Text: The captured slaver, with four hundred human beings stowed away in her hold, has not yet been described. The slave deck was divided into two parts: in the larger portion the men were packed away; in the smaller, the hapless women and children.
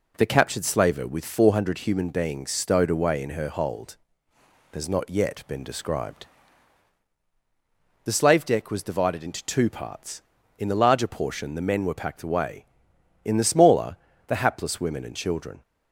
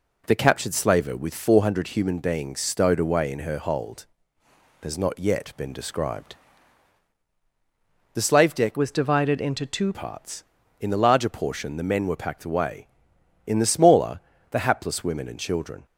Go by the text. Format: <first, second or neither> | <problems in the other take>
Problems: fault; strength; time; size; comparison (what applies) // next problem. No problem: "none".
first | changes voice from "was" to "two"; from 8.7 to 9.9 s; 1.2 s long